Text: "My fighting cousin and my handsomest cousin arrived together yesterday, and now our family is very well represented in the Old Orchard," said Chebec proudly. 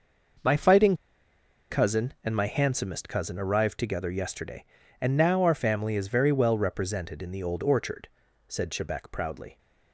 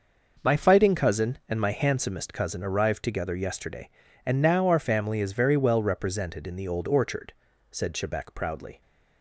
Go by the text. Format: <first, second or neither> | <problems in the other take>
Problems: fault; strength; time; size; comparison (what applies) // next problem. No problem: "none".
second | pauses between "fighting" and "cousin"; noticeable; at 0.9 s; 0.76 s long